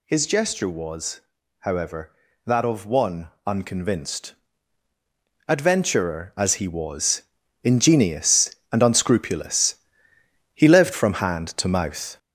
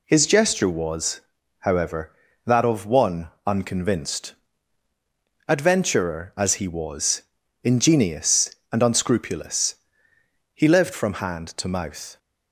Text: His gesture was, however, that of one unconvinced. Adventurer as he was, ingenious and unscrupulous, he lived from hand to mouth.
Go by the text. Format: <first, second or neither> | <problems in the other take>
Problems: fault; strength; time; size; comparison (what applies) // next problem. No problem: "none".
second | gets louder; noticeable; throughout; 5 dB // pauses between "one" and "unconvinced"; slight; at 3.2 s; 0.18 s long; slight in the second